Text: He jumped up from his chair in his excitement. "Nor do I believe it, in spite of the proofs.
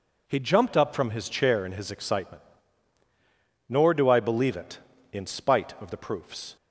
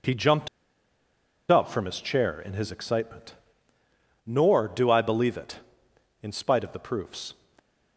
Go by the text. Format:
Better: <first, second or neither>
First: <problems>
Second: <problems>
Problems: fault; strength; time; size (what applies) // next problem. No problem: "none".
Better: first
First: none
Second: pauses between "jumped" and "up"; at 0.4 s; 1.0 s long